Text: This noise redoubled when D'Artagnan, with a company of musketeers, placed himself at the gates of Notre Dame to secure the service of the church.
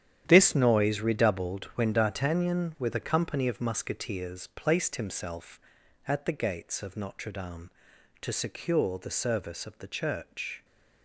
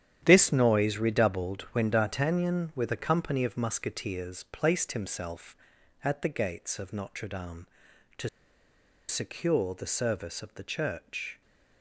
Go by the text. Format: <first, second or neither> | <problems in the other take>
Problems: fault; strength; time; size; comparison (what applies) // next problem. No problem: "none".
first | starts louder than the rest; strong; until 1.2 s; 10 dB; strong in the first // pauses between "to" and "secure"; noticeable; at 8.2 s; 0.79 s long